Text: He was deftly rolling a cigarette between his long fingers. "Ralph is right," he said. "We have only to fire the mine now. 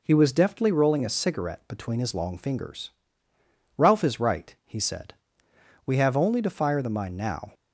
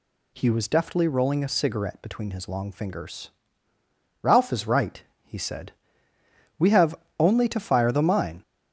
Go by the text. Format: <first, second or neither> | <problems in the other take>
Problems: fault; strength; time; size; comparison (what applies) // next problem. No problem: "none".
first | pauses between "have" and "only"; slight; at 6.9 s; 0.24 s long // stops before "now"; at 8.4 s